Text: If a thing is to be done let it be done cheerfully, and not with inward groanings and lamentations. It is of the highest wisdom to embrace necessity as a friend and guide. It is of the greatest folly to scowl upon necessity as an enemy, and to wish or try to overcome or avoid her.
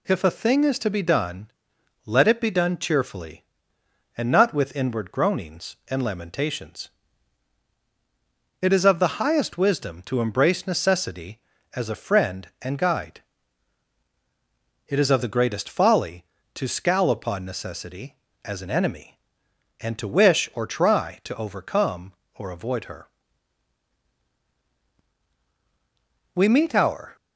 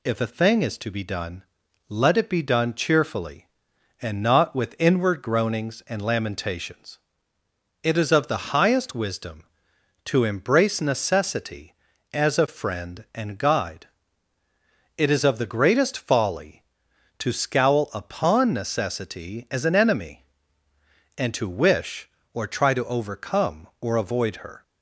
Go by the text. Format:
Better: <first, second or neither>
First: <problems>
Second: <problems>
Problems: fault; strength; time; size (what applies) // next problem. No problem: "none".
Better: second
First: pauses between "done" and "let"; noticeable; at 1.4 s; 0.58 s long // goes on to say "We meet our"; noticeable; from 26.3 s on; 0.80 s long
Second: pauses between "done" and "let"; noticeable; at 1.4 s; 0.48 s long